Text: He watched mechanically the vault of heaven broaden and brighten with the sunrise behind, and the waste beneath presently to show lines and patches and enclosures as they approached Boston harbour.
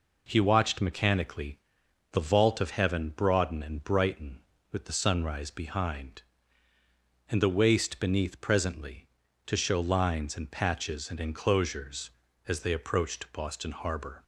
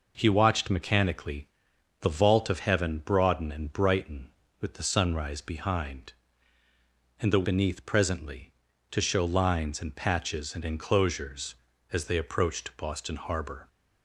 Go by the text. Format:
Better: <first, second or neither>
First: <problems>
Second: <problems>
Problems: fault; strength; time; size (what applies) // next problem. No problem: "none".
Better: first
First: pauses between "mechanically" and "the"; noticeable; at 1.6 s; 0.50 s long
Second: pauses between "mechanically" and "the"; noticeable; at 1.4 s; 0.50 s long // skips "waste"; at 7.4 s